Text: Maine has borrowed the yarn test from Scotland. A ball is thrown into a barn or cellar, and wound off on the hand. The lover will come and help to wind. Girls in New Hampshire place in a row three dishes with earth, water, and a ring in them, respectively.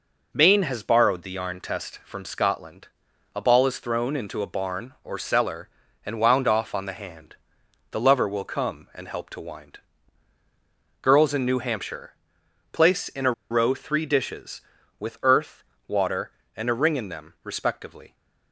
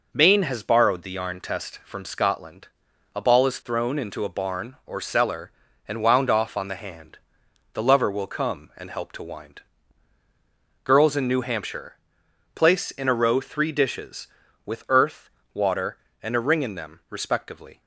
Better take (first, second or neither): second